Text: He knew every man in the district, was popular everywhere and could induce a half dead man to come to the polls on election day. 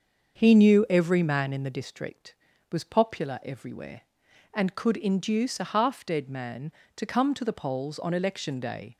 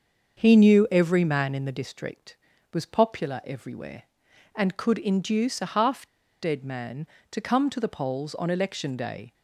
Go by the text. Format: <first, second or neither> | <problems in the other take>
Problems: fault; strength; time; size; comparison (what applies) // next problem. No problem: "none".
first | starts louder than the rest; until 1.4 s; 6.5 dB; also in the first // pauses between "half" and "dead"; at 6.0 s; 0.36 s long